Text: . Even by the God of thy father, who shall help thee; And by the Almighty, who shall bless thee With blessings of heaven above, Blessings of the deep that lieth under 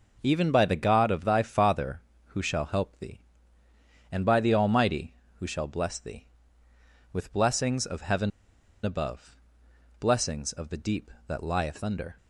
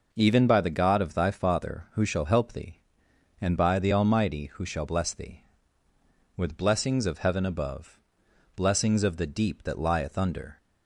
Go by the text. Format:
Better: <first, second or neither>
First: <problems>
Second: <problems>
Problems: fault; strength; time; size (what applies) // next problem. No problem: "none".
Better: second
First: pauses between "heaven" and "above"; noticeable; at 8.2 s; 0.53 s long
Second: none